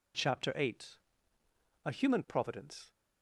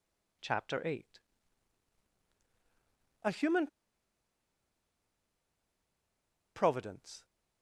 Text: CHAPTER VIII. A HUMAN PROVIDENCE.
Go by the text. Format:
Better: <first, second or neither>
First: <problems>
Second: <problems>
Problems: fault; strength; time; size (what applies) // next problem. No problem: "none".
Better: first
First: none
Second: pauses between "HUMAN" and "PROVIDENCE"; strong; at 3.6 s; 2.8 s long